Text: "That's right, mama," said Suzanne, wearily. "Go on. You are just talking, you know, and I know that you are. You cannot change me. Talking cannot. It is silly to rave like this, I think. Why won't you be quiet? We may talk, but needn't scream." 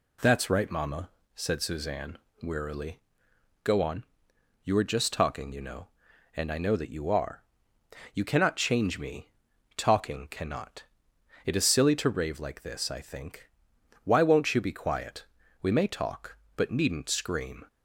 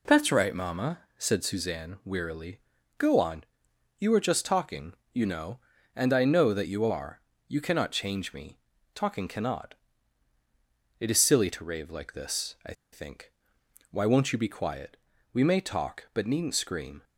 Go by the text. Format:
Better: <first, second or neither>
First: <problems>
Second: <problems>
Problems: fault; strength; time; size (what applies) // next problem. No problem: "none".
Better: first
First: none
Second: pauses between "I" and "think"; slight; at 12.7 s; 0.20 s long